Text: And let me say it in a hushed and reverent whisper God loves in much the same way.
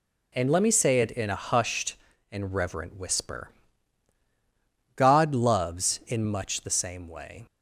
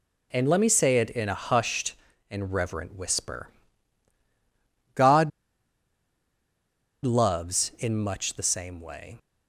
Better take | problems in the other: first | pauses between "whisper" and "God"; strong; at 3.4 s; 1.4 s long; strong in the first // pauses between "God" and "loves"; strong; at 5.3 s; 1.7 s long

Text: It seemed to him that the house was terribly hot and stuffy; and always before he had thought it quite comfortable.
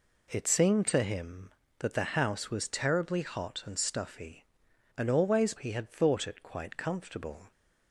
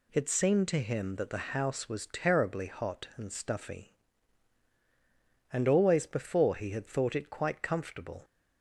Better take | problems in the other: second | skips "before"; at 5.5 s

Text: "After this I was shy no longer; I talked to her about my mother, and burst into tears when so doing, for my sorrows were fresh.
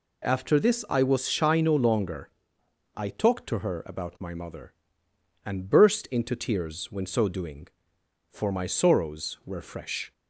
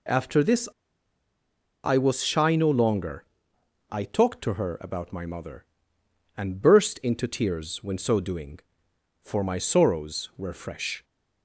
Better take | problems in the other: first | pauses between "this" and "I"; at 0.6 s; 1.1 s long

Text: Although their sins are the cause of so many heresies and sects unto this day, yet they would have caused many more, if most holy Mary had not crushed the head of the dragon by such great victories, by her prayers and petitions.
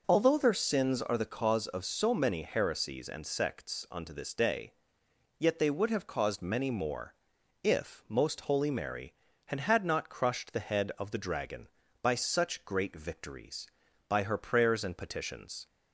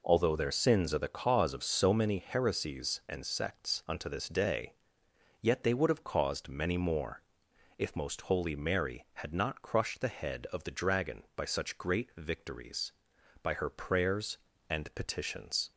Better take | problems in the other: second | says "had" twice; at 9.6 s

